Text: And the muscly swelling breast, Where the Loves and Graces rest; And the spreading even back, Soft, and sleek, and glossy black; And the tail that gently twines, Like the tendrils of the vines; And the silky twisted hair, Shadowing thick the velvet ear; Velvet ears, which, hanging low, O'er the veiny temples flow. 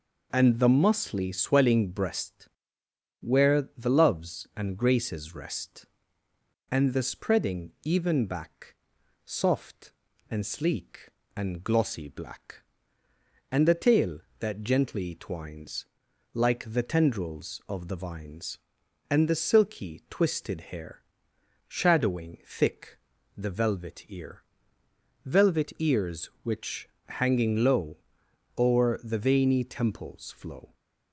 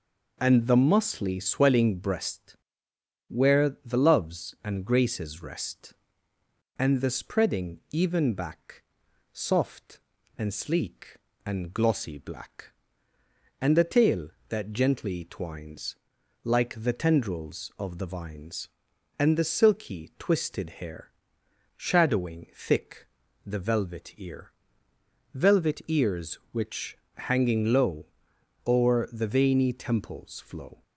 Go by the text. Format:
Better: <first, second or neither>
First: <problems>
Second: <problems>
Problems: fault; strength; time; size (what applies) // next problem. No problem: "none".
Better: neither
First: pauses between "thick" and "the"; at 22.9 s; 0.40 s long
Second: pauses between "thick" and "the"; at 23.0 s; 0.40 s long